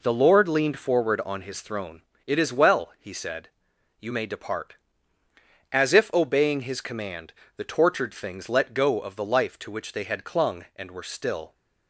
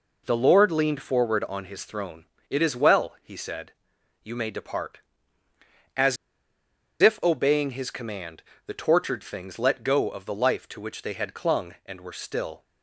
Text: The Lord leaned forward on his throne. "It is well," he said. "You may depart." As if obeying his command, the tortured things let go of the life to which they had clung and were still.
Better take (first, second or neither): first